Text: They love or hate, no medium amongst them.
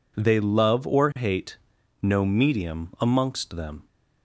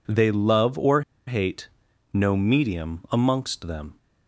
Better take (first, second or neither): first